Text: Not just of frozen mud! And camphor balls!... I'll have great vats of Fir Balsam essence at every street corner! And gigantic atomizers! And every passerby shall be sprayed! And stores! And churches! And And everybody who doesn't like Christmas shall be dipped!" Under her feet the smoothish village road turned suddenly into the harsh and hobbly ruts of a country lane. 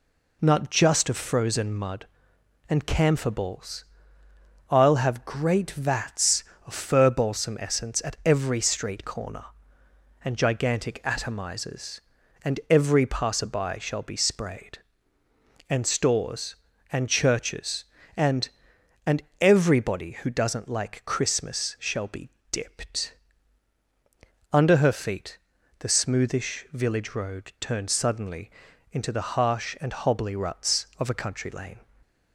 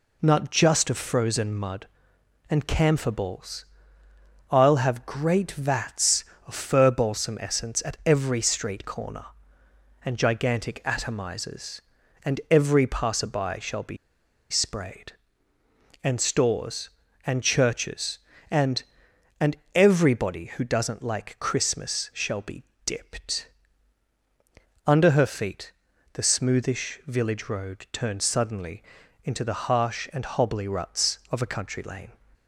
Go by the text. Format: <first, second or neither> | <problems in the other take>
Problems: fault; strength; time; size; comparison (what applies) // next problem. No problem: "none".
first | pauses between "be" and "sprayed"; noticeable; at 13.9 s; 0.54 s long // pauses between "And" and "everybody"; slight; at 19.5 s; 0.18 s long; slight in the first // pauses between "be" and "dipped"; slight; at 22.6 s; 0.22 s long; slight in the first // pauses between "feet" and "the"; at 25.7 s; 0.40 s long; also in the first // pauses between "suddenly" and "into"; at 28.8 s; 0.42 s long; also in the first